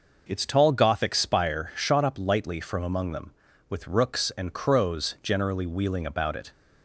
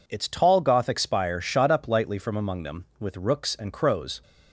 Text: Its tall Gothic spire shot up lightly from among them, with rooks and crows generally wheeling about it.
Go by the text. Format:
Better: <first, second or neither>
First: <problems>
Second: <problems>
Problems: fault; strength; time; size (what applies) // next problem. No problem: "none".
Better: first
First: none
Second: stops before "generally wheeling about it"; at 4.2 s